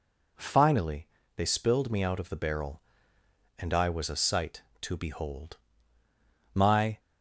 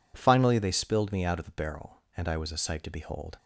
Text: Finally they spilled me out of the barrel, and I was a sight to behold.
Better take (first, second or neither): second